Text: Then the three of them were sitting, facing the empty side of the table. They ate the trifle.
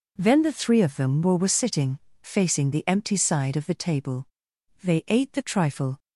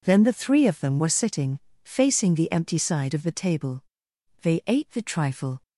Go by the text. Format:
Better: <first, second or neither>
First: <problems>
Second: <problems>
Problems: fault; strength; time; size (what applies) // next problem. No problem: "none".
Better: second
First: says "were" twice; at 1.3 s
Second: none